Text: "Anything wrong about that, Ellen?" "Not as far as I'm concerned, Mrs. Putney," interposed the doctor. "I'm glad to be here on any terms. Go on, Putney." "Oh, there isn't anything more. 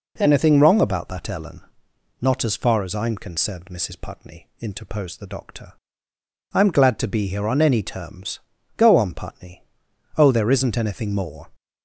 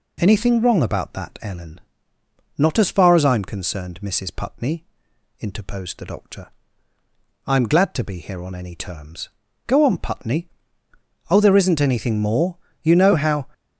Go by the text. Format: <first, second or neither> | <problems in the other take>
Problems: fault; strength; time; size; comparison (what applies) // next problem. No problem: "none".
first | goes on to say "You know how"; noticeable; from 12.8 s on; 0.66 s long